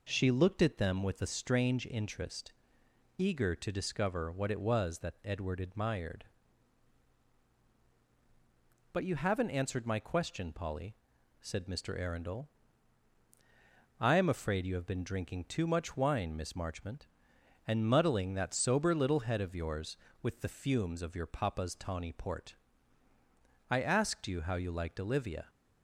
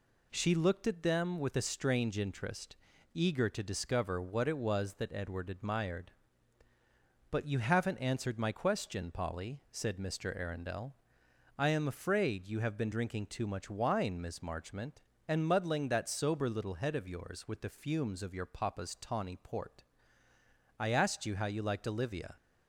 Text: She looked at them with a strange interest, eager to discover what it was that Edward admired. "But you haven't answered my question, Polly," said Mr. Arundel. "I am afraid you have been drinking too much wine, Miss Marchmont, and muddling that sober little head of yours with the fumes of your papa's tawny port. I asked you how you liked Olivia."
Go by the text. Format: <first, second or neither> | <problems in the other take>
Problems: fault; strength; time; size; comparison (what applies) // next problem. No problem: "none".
neither | none